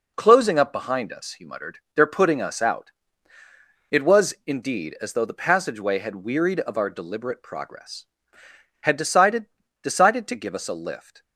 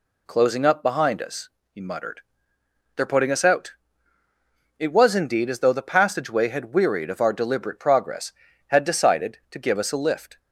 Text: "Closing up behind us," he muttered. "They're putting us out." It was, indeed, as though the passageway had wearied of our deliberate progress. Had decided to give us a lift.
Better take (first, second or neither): second